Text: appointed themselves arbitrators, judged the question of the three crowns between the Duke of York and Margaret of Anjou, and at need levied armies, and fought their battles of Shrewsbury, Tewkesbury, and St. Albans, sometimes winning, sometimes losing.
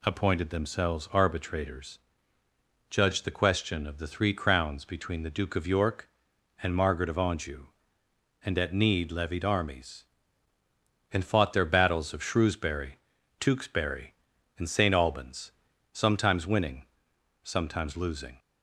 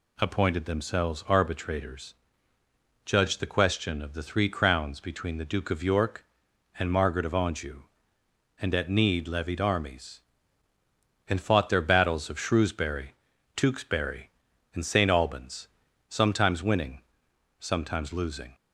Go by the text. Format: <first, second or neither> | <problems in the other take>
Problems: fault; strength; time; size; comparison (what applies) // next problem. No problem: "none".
neither | none